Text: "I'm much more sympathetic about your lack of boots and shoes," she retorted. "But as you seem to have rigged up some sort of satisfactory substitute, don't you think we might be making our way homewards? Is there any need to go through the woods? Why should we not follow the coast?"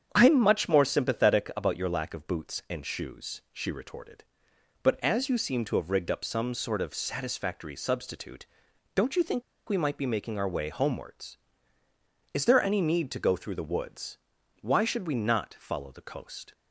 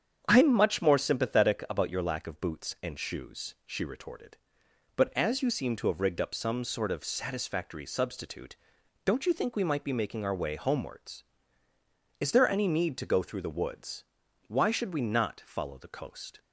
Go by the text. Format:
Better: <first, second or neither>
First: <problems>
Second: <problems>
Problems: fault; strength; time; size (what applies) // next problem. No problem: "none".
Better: second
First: starts louder than the rest; strong; until 1.1 s; 8 dB // pauses between "think" and "we"; slight; at 9.4 s; 0.26 s long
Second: starts louder than the rest; strong; until 1.2 s; 8 dB